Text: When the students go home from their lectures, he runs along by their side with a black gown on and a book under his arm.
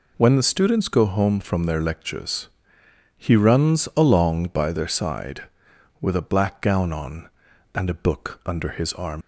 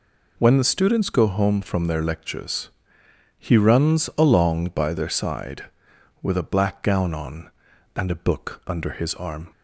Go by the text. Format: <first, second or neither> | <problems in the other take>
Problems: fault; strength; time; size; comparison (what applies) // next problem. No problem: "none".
second | leaves "arm" unfinished; at 9.2 s; 85 ms